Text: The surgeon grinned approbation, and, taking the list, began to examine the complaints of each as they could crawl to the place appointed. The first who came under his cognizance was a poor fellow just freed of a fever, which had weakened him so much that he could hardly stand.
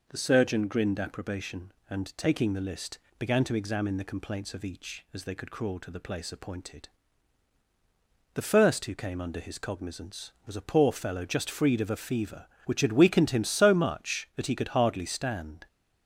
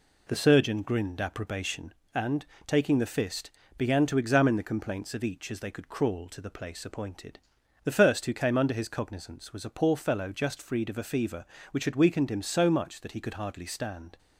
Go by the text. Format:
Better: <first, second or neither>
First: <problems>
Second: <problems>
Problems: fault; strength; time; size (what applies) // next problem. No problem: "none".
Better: first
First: none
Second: says "fist" for "list"; at 3.0 s